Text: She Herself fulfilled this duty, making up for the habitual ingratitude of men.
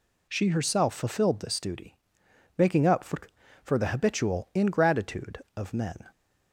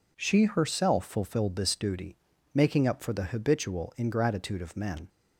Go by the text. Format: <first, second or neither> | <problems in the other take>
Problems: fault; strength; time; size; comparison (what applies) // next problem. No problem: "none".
second | says "for" twice; at 3.6 s